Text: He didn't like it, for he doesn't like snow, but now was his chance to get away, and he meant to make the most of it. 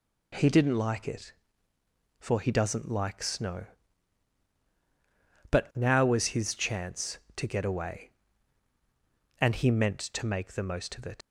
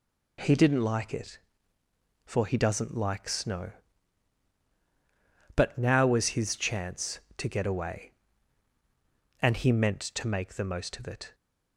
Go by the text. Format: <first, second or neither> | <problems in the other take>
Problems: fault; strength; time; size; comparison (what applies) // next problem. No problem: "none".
second | leaves "it" unfinished; at 11.2 s; 125 ms